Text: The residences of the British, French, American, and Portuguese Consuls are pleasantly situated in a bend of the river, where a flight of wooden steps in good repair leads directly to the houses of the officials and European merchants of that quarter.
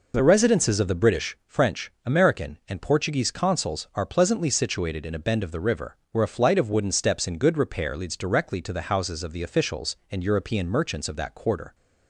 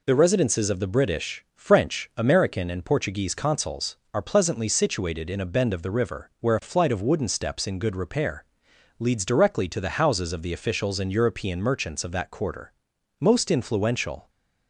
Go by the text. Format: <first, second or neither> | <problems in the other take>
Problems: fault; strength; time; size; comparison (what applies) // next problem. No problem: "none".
first | pauses between "repair" and "leads"; noticeable; at 8.4 s; 0.54 s long // goes on to say "Most influential"; noticeable; from 13.1 s on; 1.1 s long